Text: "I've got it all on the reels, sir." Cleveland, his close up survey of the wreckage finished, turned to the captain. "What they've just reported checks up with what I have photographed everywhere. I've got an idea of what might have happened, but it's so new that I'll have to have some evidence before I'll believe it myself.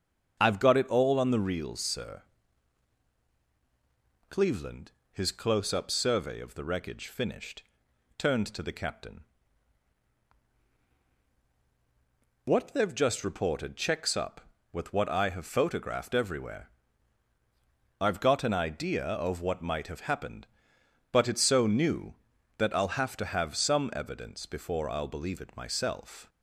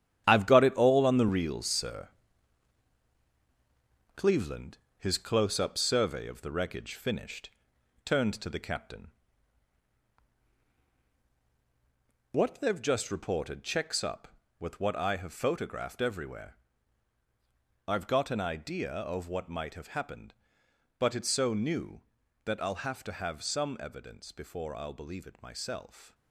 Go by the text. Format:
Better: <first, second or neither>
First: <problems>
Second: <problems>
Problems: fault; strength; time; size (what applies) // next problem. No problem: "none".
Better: first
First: starts louder than the rest; strong; until 1.4 s; 7 dB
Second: gets quieter; strong; throughout; 9.5 dB // starts louder than the rest; strong; until 1.2 s; 10 dB